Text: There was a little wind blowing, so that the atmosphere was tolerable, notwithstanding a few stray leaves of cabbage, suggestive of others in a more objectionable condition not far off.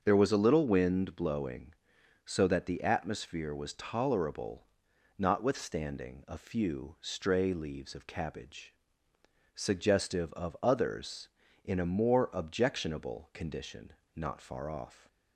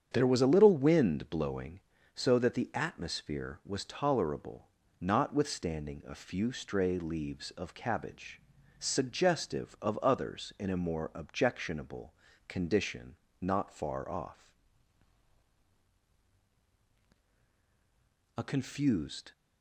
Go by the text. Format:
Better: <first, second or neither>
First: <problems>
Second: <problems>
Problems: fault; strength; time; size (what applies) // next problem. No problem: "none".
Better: first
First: starts louder than the rest; until 1.0 s; 6.5 dB // pauses between "condition" and "not"; slight; at 13.9 s; 0.20 s long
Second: starts louder than the rest; strong; until 1.1 s; 7.5 dB // pauses between "objectionable" and "condition"; slight; at 12.1 s; 0.36 s long // pauses between "condition" and "not"; slight; at 13.1 s; 0.24 s long // goes on to say "A confused"; noticeable; from 18.3 s on; 0.96 s long